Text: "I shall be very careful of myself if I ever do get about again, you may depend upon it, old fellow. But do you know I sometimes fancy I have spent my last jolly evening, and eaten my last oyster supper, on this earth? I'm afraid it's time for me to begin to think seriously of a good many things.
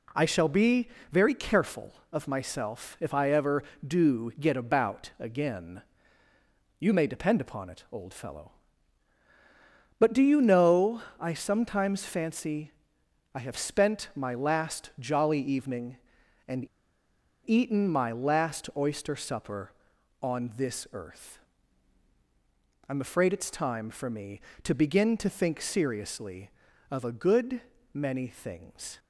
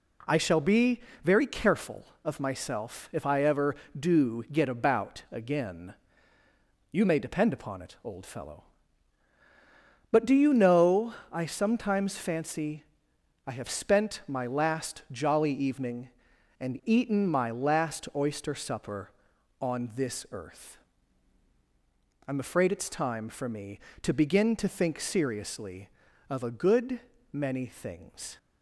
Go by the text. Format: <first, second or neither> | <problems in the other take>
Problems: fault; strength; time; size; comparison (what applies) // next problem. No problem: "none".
second | pauses between "be" and "very"; slight; at 0.8 s; 0.22 s long; slight in the second // pauses between "know" and "I"; slight; at 11.0 s; 0.18 s long; slight in the second // pauses between "fancy" and "I"; noticeable; at 12.7 s; 0.64 s long; noticeable in the second // pauses between "and" and "eaten"; noticeable; at 16.6 s; 0.79 s long // pauses between "good" and "many"; slight; at 27.6 s; 0.32 s long; slight in the second